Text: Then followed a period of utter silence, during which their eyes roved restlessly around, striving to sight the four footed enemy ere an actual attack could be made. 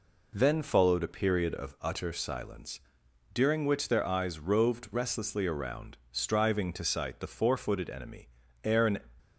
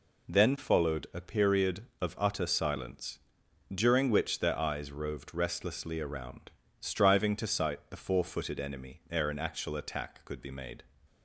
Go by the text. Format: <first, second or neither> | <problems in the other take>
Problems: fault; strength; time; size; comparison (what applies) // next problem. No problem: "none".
second | pauses between "enemy" and "ere"; slight; at 8.2 s; 0.36 s long // stops before "actual attack could be made"; at 9.1 s